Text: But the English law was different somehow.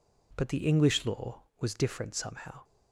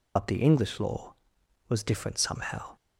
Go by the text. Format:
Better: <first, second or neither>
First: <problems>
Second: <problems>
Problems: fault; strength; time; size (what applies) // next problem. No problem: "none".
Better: first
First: none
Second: loses the start of "But"; at 0.1 s; 60 ms